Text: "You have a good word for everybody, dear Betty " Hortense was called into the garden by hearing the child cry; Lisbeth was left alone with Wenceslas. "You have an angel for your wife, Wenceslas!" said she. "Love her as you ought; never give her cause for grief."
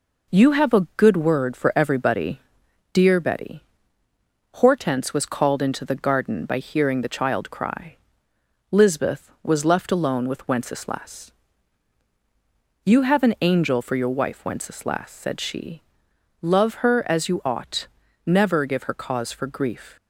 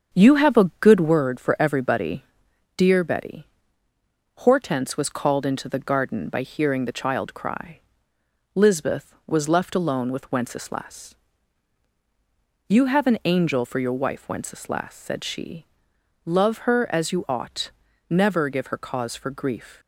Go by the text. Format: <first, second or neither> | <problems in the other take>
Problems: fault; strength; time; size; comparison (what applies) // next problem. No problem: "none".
first | starts louder than the rest; until 1.3 s; 6.5 dB